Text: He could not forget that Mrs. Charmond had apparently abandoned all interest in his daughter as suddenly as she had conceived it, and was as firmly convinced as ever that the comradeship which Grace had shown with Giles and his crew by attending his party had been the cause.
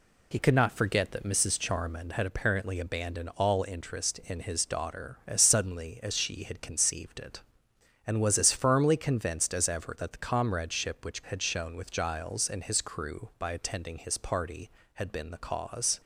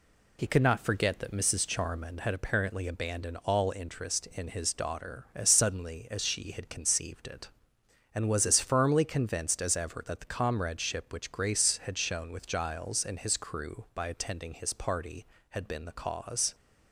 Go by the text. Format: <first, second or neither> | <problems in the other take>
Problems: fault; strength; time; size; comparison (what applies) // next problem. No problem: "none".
second | skips "Grace"; at 11.2 s